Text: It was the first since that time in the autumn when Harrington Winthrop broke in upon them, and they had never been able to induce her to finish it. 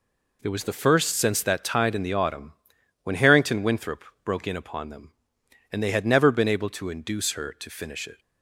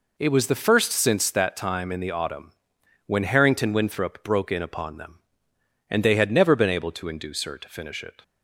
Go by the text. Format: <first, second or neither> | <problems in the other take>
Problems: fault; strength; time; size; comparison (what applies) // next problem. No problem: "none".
second | says "tide" for "time"; at 1.6 s // pauses between "autumn" and "when"; noticeable; at 2.5 s; 0.50 s long; noticeable in the second // pauses between "Winthrop" and "broke"; slight; at 4.0 s; 0.20 s long